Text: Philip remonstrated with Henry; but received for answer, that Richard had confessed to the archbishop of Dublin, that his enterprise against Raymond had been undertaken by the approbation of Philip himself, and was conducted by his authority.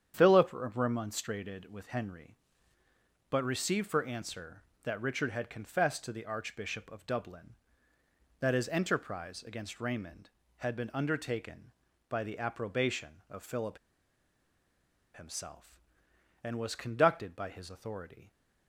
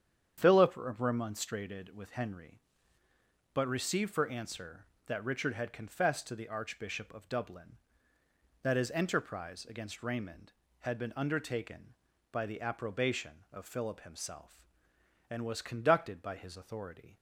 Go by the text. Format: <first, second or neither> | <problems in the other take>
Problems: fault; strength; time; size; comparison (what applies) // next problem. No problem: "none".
second | starts louder than the rest; strong; until 1.1 s; 8.5 dB; strong in the second // pauses between "Philip" and "himself"; strong; at 13.7 s; 1.3 s long